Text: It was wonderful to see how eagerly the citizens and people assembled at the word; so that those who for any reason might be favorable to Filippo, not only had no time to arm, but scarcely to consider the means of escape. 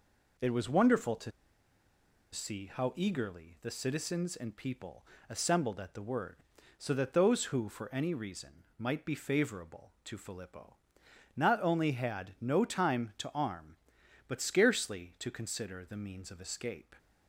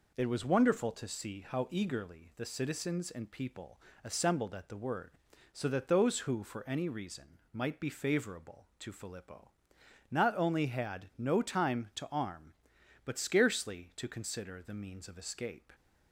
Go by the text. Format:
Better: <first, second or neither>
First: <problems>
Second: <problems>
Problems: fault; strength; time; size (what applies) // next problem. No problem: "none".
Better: second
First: pauses between "to" and "see"; at 1.3 s; 1.0 s long // pauses between "people" and "assembled"; slight; at 5.0 s; 0.24 s long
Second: pauses between "people" and "assembled"; slight; at 3.7 s; 0.24 s long